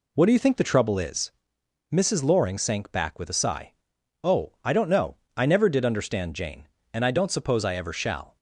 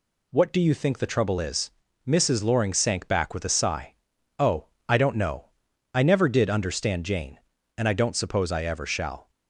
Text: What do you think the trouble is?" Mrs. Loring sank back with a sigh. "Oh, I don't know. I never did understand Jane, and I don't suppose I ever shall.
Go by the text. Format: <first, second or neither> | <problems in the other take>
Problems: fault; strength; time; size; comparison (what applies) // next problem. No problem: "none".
neither | none